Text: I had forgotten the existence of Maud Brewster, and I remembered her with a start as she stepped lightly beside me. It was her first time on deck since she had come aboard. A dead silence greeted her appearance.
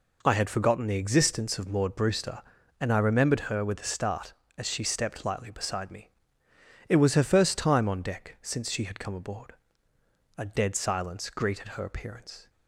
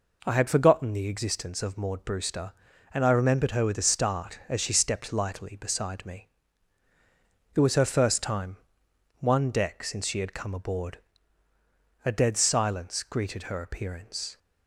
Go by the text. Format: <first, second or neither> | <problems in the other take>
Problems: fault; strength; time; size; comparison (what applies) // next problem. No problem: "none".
first | says "one" for "on"; at 9.2 s